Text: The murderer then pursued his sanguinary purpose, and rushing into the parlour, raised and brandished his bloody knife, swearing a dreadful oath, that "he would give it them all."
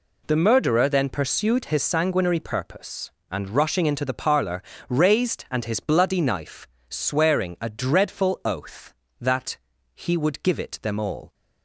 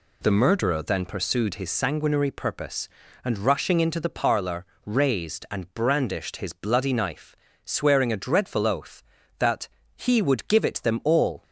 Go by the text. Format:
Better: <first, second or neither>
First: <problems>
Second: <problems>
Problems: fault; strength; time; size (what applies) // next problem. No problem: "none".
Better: second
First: skips "brandished"; at 5.6 s // pauses between "that" and "he"; slight; at 9.5 s; 0.36 s long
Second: pauses between "that" and "he"; slight; at 9.6 s; 0.30 s long